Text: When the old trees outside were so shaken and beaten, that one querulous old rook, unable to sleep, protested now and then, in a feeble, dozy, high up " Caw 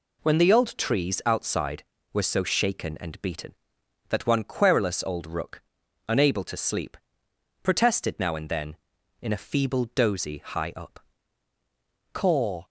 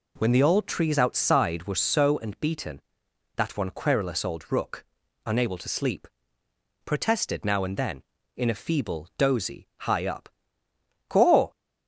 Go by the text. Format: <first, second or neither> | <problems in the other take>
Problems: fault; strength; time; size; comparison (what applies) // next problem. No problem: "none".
first | skips "shaken"; at 2.1 s